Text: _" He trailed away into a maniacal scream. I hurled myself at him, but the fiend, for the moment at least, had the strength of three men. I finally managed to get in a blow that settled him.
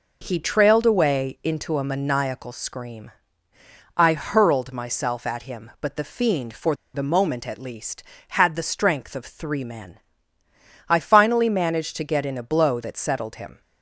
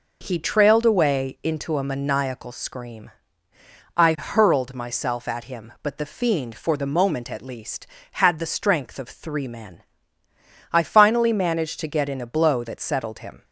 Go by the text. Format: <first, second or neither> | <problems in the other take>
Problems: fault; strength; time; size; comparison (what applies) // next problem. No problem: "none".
second | pauses between "for" and "the"; slight; at 6.7 s; 0.18 s long